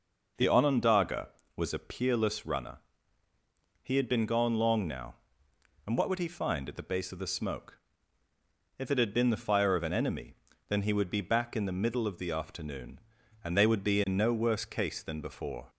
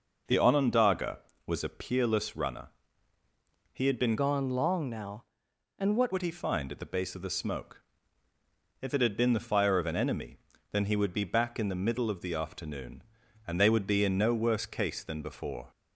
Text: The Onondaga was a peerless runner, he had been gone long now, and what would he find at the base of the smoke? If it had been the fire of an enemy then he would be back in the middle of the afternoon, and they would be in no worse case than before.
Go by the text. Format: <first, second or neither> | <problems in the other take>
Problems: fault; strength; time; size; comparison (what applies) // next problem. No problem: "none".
first | changes voice from "gone" to "what"; from 4.1 to 6.1 s; 2.0 s long // pauses between "enemy" and "then"; slight; at 10.3 s; 0.34 s long; slight in the first